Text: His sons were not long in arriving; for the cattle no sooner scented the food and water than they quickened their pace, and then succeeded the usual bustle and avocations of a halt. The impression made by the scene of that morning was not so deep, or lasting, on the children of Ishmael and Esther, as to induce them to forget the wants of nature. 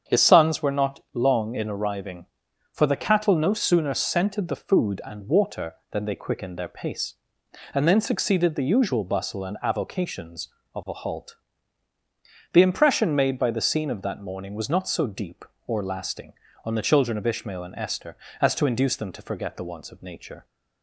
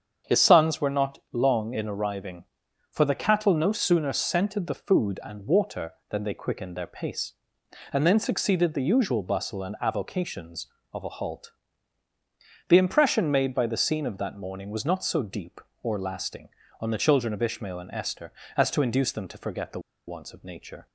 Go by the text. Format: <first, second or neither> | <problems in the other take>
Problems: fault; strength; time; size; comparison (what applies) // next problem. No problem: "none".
first | starts louder than the rest; strong; until 1.4 s; 7.5 dB; strong in the first // pauses between "the" and "wants"; slight; at 19.8 s; 0.27 s long